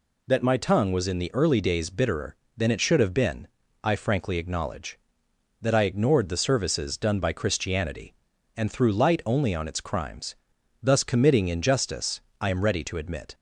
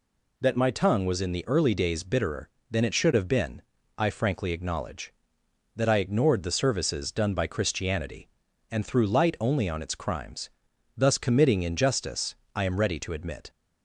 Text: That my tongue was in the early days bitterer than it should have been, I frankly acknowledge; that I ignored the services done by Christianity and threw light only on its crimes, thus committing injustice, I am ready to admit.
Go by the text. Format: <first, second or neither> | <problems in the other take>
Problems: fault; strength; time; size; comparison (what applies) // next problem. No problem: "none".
neither | none